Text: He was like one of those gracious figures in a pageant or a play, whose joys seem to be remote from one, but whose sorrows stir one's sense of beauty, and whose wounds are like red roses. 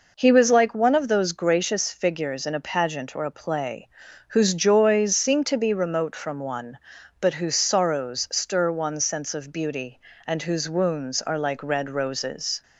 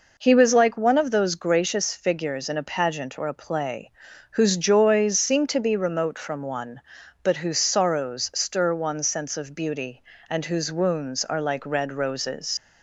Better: first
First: none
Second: leaves "roses" unfinished; at 12.5 s; 75 ms

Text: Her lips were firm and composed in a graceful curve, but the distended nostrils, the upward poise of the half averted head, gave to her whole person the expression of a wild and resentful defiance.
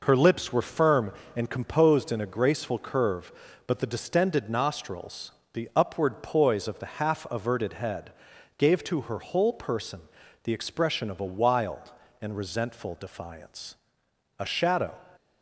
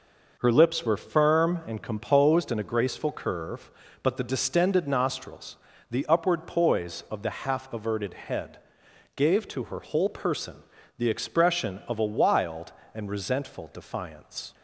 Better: second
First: pauses between "person" and "the"; at 10.0 s; 0.42 s long // goes on to say "A shadow"; from 14.3 s on; 0.54 s long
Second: pauses between "person" and "the"; at 10.6 s; 0.38 s long

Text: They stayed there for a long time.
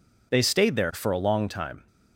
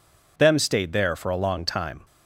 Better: first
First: none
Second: says "Them" for "They"; at 0.3 s

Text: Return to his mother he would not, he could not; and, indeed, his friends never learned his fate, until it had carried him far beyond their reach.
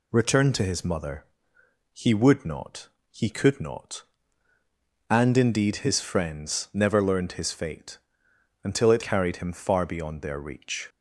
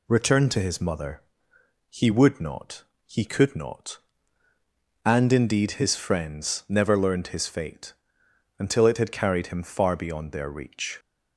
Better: second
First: pauses between "mother" and "he"; noticeable; at 1.2 s; 0.68 s long // skips "had"; at 9.0 s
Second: pauses between "mother" and "he"; noticeable; at 1.2 s; 0.68 s long

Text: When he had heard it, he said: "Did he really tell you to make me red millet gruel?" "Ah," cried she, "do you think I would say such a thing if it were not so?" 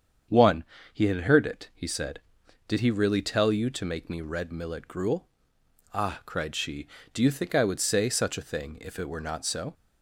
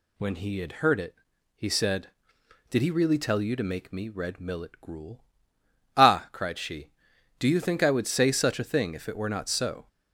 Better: second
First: starts louder than the rest; strong; until 1.6 s; 7.5 dB // says "One" for "When"; at 0.2 s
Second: none

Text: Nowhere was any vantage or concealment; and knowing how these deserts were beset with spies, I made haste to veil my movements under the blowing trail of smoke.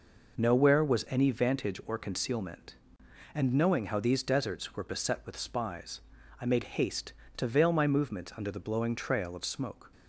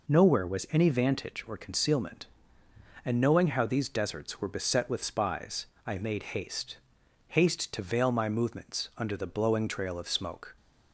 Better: first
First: none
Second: says "haste" twice; at 7.2 s

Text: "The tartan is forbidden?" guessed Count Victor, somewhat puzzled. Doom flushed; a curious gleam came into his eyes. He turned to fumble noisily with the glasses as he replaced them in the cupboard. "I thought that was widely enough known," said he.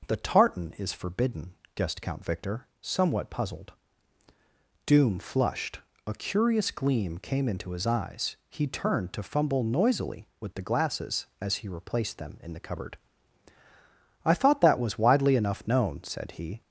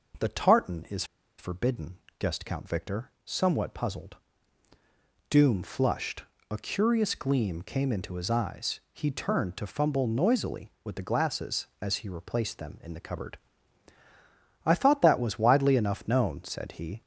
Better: first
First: none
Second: pauses between "is" and "forbidden"; slight; at 1.0 s; 0.34 s long

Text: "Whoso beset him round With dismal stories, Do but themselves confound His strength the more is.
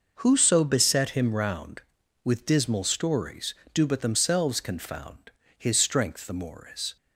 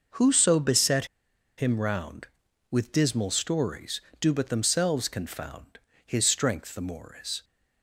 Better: first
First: pauses between "confound" and "His"; slight; at 5.2 s; 0.28 s long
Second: pauses between "beset" and "him"; noticeable; at 1.0 s; 0.52 s long // pauses between "confound" and "His"; slight; at 5.7 s; 0.28 s long

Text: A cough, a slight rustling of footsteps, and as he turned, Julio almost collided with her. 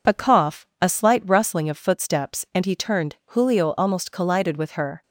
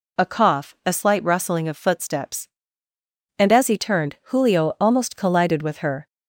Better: second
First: skips "as"; at 2.6 s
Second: none

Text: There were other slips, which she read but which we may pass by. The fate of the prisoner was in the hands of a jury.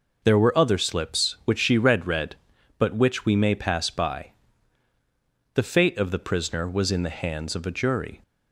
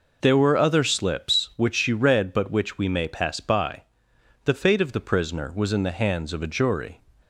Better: second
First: says "read" twice; at 2.0 s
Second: none

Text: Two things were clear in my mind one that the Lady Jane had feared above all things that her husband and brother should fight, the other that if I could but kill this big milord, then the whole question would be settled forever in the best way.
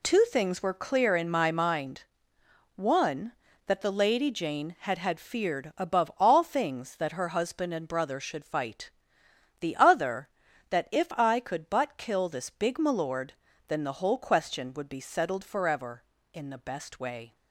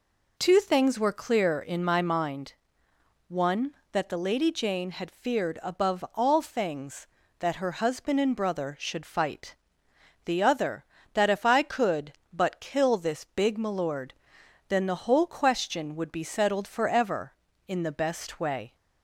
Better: second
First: pauses between "mind" and "one"; noticeable; at 2.0 s; 0.72 s long // says "had" twice; at 4.9 s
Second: pauses between "mind" and "one"; noticeable; at 2.5 s; 0.76 s long

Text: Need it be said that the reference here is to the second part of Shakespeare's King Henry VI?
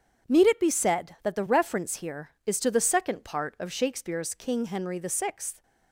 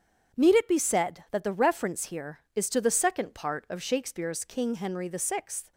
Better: neither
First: starts louder than the rest; strong; until 1.3 s; 8 dB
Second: starts louder than the rest; strong; until 1.4 s; 8 dB

